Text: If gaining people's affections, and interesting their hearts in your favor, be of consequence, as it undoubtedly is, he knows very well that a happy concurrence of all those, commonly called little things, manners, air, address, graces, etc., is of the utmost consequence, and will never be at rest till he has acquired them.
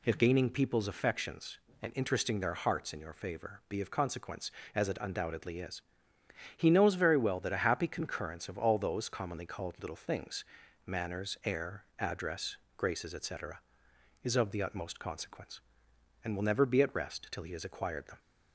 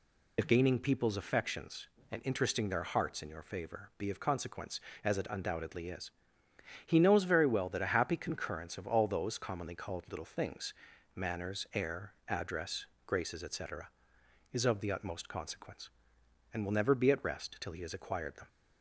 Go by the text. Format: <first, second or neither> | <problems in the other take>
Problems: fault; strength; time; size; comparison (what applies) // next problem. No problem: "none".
first | loses the start of "If"; at 0.3 s; 60 ms